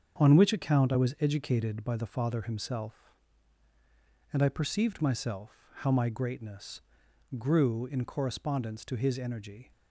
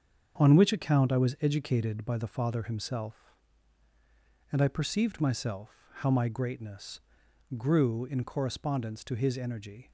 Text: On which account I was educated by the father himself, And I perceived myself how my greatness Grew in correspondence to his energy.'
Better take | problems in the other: neither | starts louder than the rest; strong; the same in both // pauses between "myself" and "how"; slight; the same in both // pauses between "greatness" and "Grew"; noticeable; the same in both

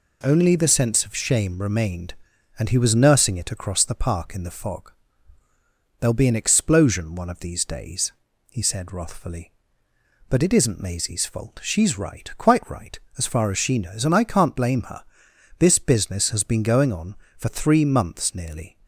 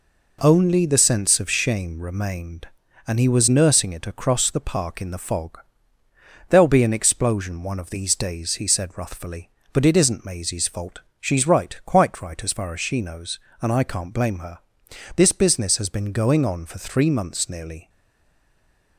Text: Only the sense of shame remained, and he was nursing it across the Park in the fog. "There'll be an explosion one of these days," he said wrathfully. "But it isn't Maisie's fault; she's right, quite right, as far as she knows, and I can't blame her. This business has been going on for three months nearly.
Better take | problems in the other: first | stays silent after the last word; from 17.8 s on; 1.1 s long

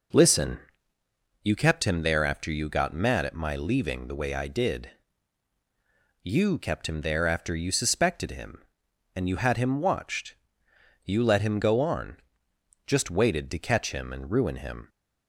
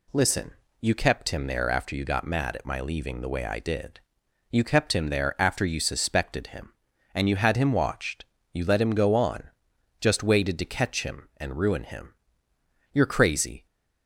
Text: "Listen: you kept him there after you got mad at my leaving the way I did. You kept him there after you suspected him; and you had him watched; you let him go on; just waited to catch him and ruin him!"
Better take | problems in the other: first | goes on to say "You're crazy"; noticeable; from 12.9 s on; 0.72 s long

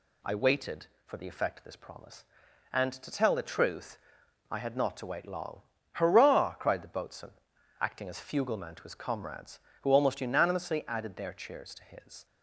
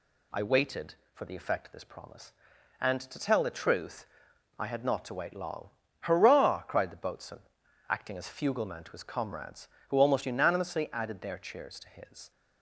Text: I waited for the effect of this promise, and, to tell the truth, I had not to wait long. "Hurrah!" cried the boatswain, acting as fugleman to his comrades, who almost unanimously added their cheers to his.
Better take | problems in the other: neither | none

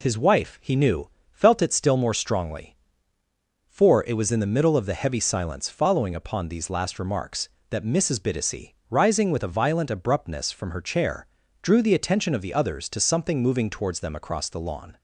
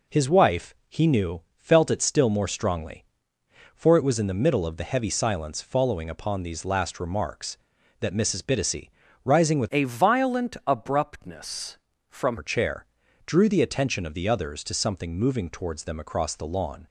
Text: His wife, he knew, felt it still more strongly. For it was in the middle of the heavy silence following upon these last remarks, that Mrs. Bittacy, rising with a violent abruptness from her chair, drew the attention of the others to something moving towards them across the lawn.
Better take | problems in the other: first | changes voice from "a" to "from"; from 9.7 to 12.3 s; 2.6 s long

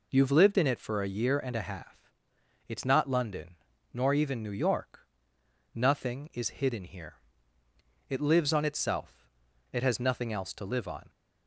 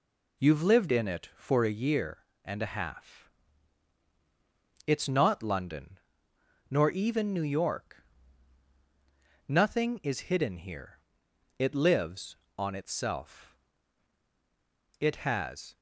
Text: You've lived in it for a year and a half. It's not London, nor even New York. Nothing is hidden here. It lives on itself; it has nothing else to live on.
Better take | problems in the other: first | stops before "nothing else to live on"; at 15.7 s

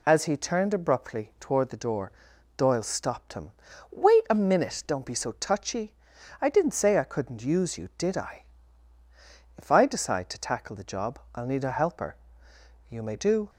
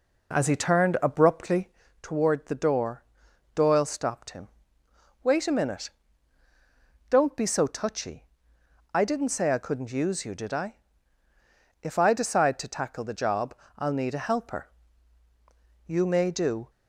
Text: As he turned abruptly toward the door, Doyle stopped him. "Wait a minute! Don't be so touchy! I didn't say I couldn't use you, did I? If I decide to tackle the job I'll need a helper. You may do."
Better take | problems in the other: first | starts louder than the rest; noticeable; until 1.9 s; 4 dB // pauses between "abruptly" and "toward"; slight; at 1.6 s; 0.34 s long // pauses between "job" and "I'll"; slight; at 13.5 s; 0.24 s long; slight in the first

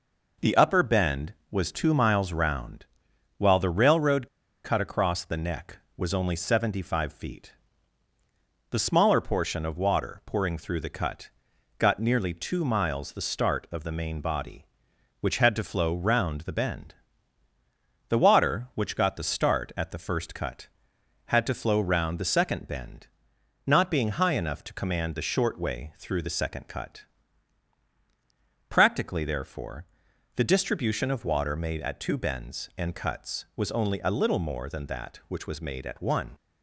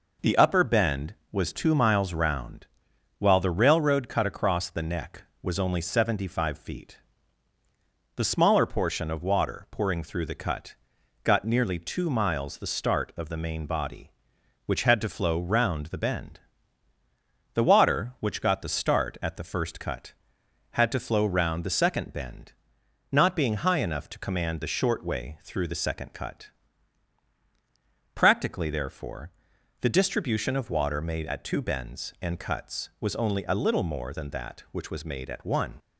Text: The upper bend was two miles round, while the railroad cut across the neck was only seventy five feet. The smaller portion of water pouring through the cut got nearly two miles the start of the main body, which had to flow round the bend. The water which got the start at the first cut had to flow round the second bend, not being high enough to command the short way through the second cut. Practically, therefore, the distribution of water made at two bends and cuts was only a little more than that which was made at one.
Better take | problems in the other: second | pauses between "railroad" and "cut"; at 4.2 s; 0.36 s long // pauses between "cut" and "got"; noticeable; at 11.2 s; 0.48 s long; noticeable in the second

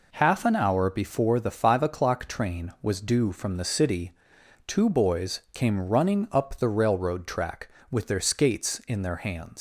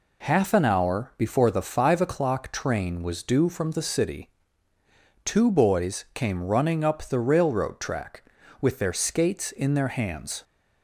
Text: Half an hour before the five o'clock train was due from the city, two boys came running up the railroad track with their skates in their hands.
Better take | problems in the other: second | leaves "hands" unfinished; at 9.5 s; 110 ms

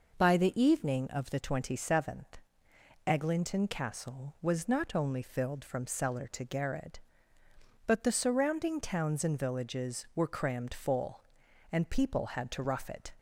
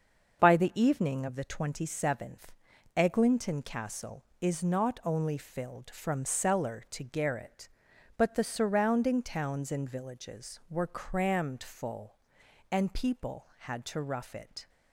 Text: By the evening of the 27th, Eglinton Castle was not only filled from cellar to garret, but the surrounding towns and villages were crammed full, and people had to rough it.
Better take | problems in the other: first | starts louder than the rest; until 1.4 s; 6.5 dB // says "is" for "was"; at 4.4 s

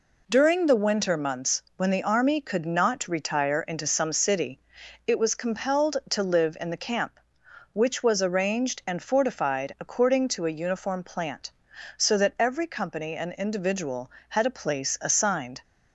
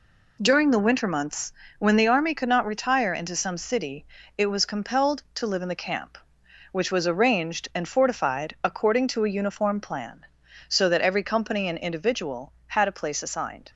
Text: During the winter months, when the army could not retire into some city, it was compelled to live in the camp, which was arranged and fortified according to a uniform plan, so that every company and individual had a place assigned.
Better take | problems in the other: second | says "plant" for "plan"; at 11.0 s

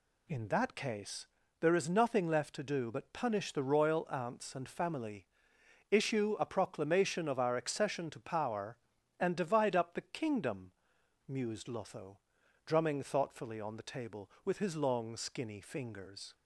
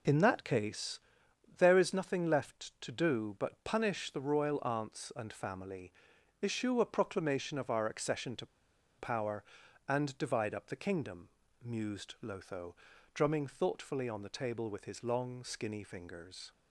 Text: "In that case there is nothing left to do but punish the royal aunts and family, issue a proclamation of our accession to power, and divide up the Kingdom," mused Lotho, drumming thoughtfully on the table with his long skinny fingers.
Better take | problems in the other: first | pauses between "case" and "there"; noticeable; at 1.0 s; 0.58 s long; slight in the first // pauses between "to" and "power"; noticeable; at 8.4 s; 0.52 s long

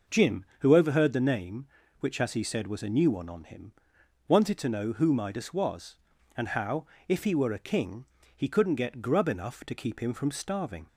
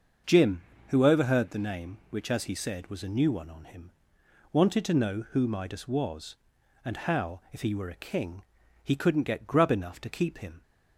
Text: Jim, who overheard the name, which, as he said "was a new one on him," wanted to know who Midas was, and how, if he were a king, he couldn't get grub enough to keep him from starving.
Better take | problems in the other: first | starts louder than the rest; until 1.5 s; 6 dB // stops before "from starving"; at 10.6 s

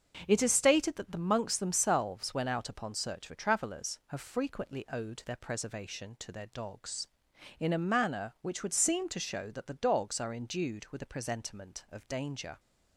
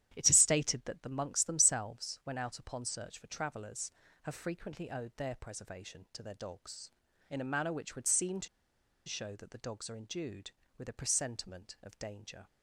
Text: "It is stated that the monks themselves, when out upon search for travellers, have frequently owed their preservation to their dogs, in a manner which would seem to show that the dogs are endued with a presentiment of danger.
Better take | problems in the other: first | starts louder than the rest; strong; until 1.1 s; 11 dB; also in the first // pauses between "to" and "show"; noticeable; at 8.4 s; 0.59 s long

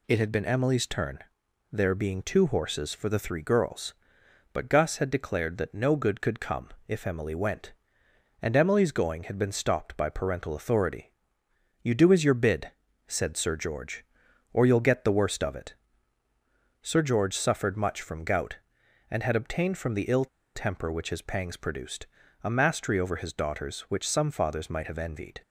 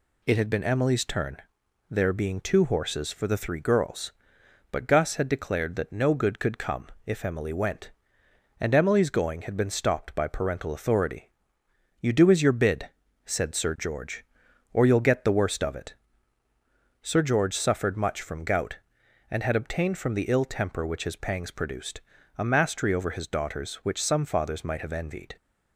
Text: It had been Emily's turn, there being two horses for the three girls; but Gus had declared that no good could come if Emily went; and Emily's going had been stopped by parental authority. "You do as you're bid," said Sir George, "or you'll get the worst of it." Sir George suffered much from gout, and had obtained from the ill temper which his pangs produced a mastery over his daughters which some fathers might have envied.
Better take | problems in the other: second | pauses between "come" and "if"; slight; at 6.6 s; 0.20 s long; slight in the second // pauses between "ill" and "temper"; slight; at 20.2 s; 0.28 s long // pauses between "produced" and "a"; at 22.0 s; 0.38 s long; also in the second

